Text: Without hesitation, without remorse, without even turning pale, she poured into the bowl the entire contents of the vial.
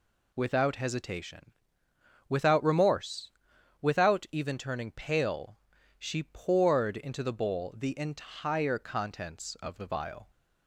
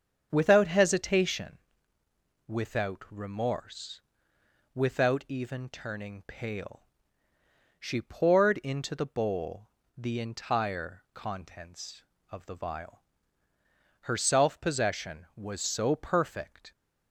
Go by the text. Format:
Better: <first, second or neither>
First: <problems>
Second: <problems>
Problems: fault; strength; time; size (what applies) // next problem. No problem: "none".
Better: first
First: none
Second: starts louder than the rest; strong; until 1.3 s; 7.5 dB // pauses between "bowl" and "the"; slight; at 9.6 s; 0.30 s long // goes on to say "Her self possession was so perfect"; strong; from 14.0 s on; 2.7 s long